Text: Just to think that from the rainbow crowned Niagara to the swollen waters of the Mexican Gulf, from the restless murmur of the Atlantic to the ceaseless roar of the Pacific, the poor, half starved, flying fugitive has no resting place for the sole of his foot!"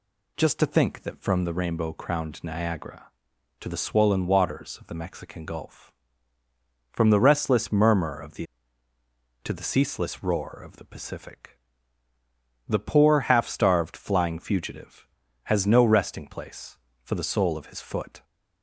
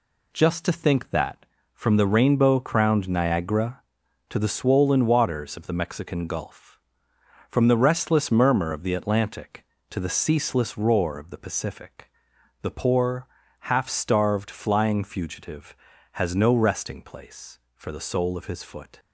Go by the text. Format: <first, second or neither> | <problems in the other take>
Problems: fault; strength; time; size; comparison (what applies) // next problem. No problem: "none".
second | skips "Atlantic"; at 8.9 s